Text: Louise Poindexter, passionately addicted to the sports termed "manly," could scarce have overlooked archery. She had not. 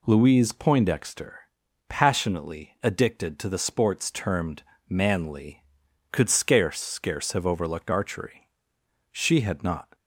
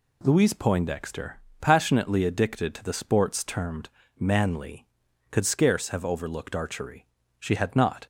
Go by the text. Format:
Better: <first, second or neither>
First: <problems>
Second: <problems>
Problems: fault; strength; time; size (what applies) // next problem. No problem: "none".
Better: second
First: pauses between "termed" and "manly"; slight; at 4.6 s; 0.26 s long // says "scarce" twice; at 6.8 s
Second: pauses between "termed" and "manly"; slight; at 3.8 s; 0.30 s long